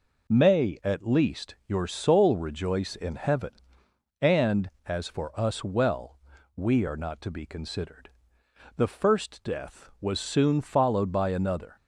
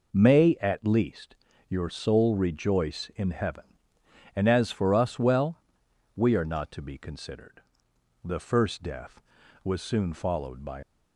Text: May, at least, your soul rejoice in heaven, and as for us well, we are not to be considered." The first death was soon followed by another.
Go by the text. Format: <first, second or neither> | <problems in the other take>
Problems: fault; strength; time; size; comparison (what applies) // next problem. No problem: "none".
first | stops before "another"; at 10.8 s